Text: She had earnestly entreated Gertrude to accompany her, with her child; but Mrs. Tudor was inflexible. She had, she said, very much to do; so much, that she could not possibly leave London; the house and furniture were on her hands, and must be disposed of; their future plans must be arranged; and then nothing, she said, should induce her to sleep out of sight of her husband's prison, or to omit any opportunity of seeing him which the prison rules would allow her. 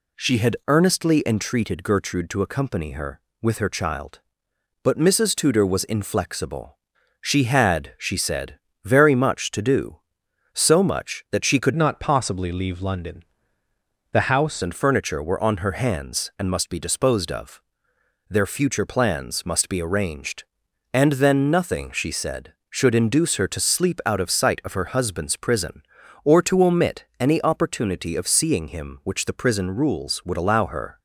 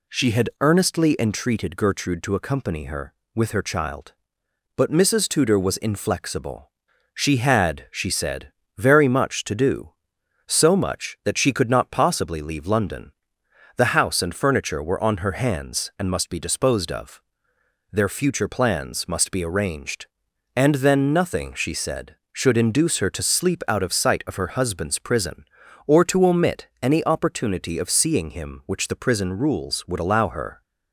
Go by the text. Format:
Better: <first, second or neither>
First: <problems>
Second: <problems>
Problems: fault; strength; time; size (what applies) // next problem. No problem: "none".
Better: second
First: changes voice from "not" to "house"; from 11.7 to 14.6 s; 2.9 s long // pauses between "omit" and "any"; slight; at 27.0 s; 0.16 s long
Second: pauses between "omit" and "any"; slight; at 26.6 s; 0.16 s long